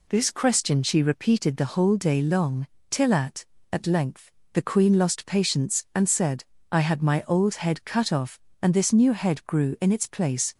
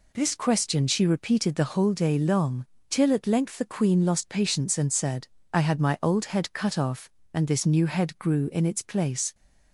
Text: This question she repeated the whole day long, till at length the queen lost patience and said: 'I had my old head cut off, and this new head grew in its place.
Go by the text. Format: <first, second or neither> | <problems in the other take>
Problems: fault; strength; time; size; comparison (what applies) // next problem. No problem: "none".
second | says "at" twice; at 3.7 s // pauses between "length" and "the"; slight; at 4.2 s; 0.24 s long